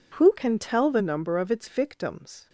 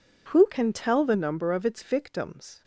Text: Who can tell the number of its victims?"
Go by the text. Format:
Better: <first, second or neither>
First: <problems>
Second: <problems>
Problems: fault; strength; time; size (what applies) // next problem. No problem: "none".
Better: neither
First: none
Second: none